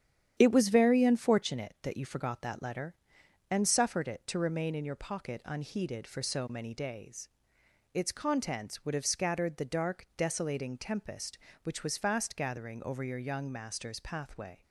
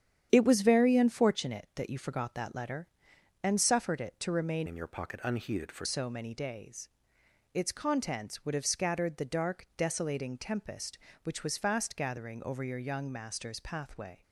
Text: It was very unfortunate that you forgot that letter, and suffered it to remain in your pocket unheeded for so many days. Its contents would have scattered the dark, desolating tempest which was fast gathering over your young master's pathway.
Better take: first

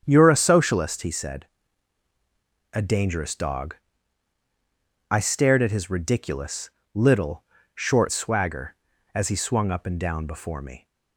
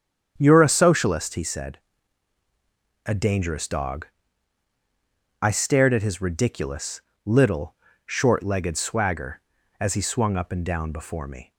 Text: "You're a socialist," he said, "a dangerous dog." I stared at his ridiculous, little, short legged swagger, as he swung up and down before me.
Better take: second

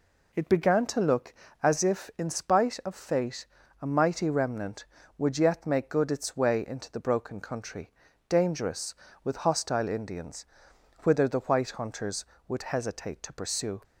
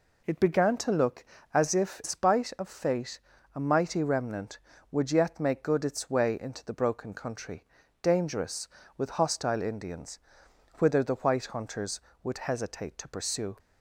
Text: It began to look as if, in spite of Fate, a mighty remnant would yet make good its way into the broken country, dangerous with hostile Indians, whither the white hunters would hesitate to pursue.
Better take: first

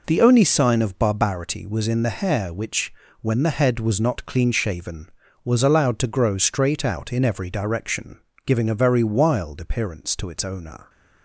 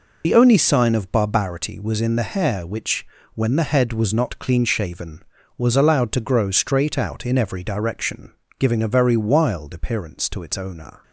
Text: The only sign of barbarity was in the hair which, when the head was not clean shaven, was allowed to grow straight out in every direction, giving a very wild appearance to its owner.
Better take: first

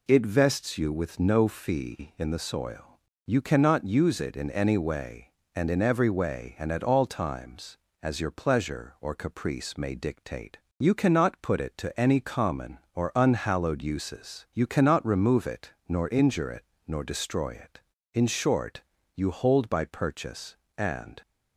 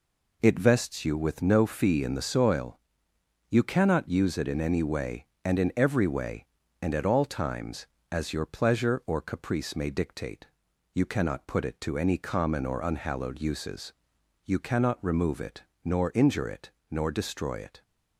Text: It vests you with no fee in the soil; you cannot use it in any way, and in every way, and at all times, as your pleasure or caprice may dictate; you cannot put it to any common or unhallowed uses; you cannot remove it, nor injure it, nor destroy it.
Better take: second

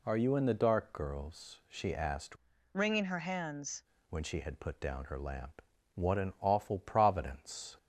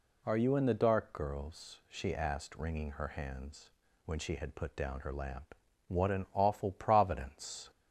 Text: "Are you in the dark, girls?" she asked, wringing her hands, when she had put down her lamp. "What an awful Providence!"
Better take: second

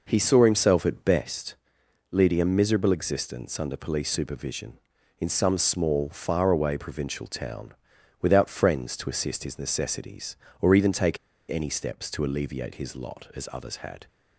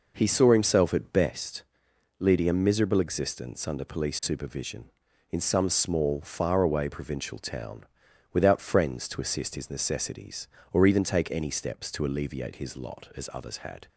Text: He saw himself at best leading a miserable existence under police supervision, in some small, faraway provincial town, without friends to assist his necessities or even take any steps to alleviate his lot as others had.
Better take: second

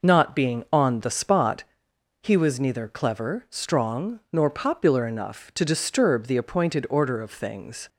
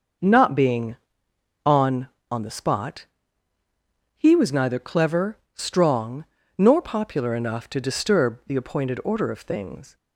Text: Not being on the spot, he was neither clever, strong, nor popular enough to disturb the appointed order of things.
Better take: first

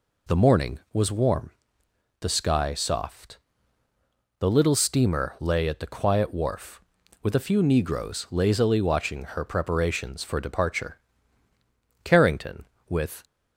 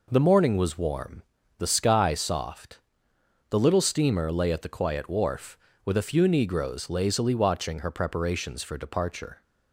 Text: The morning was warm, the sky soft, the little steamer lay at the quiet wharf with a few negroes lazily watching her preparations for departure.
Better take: second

